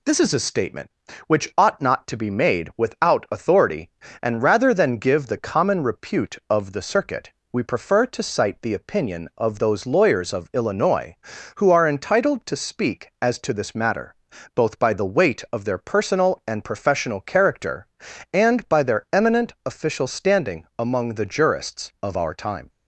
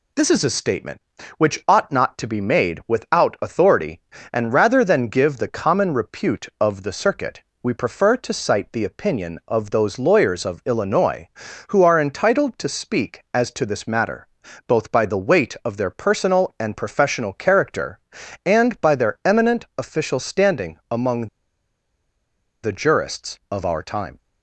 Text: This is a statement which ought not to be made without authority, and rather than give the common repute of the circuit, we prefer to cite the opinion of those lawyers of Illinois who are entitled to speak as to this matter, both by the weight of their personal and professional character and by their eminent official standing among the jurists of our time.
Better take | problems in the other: first | pauses between "among" and "the"; strong; at 21.2 s; 1.3 s long

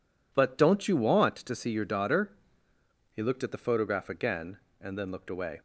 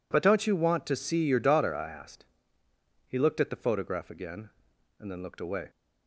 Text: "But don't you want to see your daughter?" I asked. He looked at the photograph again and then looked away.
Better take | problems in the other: second | skips "I asked"; at 2.7 s

